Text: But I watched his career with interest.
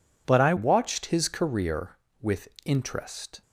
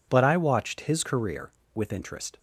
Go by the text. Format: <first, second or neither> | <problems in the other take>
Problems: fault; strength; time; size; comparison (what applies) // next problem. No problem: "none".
second | changes voice at "watched"; from 0.5 s on; 2.9 s long // pauses between "with" and "interest"; slight; at 2.4 s; 0.16 s long